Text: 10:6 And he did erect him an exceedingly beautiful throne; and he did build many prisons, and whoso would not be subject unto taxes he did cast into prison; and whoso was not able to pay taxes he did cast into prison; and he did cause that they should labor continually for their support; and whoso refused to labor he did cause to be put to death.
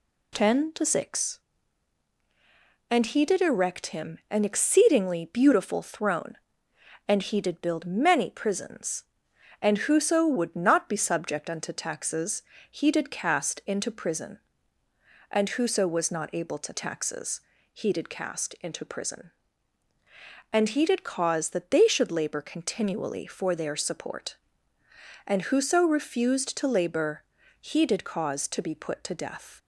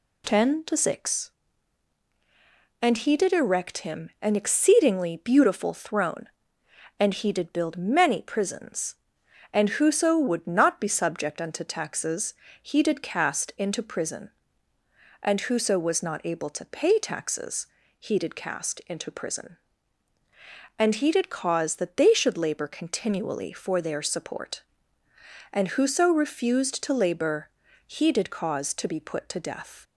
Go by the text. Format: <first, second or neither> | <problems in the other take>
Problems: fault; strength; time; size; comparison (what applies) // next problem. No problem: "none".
second | pauses between "taxes" and "he"; slight; at 12.4 s; 0.30 s long; slight in the second // skips "pay"; at 16.7 s // pauses between "taxes" and "he"; slight; at 17.4 s; 0.32 s long; slight in the second // pauses between "labor" and "he"; slight; at 27.2 s; 0.36 s long; slight in the second